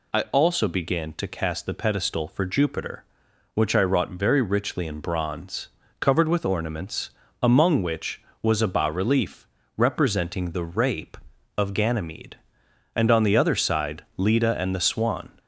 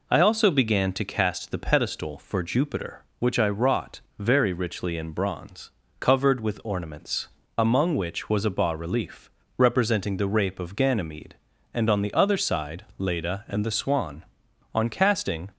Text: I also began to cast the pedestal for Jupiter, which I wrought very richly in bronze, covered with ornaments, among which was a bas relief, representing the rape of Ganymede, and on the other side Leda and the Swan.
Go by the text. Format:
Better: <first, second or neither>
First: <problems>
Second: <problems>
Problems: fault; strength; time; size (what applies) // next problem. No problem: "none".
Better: first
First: none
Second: pauses between "wrought" and "very"; slight; at 3.9 s; 0.18 s long // goes on to say "On casting"; noticeable; from 14.7 s on; 0.76 s long